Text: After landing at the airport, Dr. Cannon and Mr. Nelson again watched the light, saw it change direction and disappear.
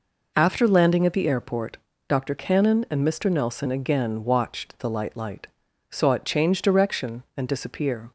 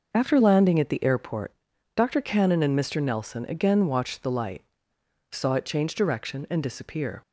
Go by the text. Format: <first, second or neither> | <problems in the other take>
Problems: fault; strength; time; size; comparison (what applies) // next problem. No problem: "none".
second | says "light" twice; at 5.1 s